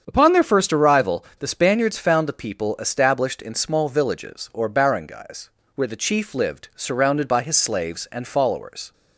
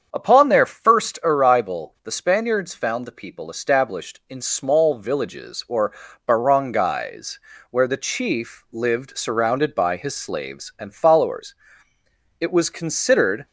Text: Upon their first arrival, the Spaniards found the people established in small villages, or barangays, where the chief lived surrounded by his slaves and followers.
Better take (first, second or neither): first